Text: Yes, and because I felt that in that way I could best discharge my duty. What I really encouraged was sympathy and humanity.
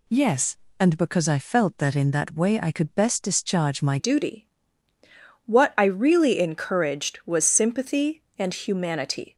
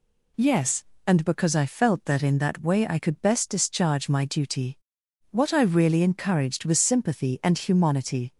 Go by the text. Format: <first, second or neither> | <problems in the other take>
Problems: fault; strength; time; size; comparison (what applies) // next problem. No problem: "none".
second | changes voice at "duty"; from 3.9 s on; 5.4 s long